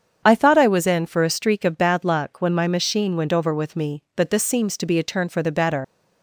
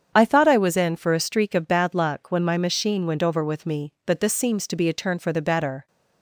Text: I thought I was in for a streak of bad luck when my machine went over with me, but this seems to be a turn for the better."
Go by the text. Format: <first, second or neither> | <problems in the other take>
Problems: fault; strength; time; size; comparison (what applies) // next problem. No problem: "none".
second | starts louder than the rest; strong; until 1.2 s; 7.5 dB; strong in the second // leaves "better" unfinished; at 5.8 s; 120 ms